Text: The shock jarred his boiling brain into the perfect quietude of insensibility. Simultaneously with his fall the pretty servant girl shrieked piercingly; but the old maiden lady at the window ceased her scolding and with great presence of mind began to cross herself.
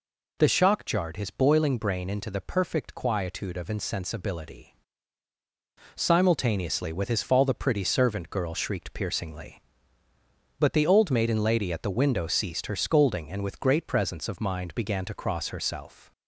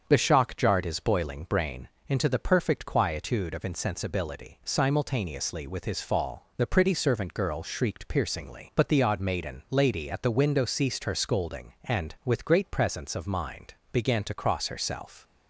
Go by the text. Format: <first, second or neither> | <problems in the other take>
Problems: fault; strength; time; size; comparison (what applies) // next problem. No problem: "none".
first | starts louder than the rest; until 1.0 s; 7 dB // pauses between "brain" and "into"; slight; at 1.8 s; 0.20 s long // says "odd" for "old"; at 9.0 s // pauses between "mind" and "began"; slight; at 13.7 s; 0.18 s long